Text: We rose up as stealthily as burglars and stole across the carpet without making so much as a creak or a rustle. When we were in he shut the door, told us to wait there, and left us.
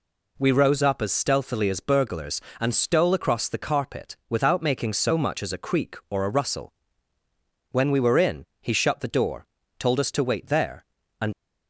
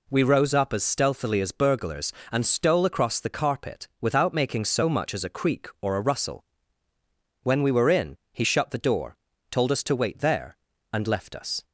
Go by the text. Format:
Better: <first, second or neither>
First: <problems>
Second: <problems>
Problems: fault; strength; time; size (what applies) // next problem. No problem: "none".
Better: second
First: stops before "left us"; at 11.3 s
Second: none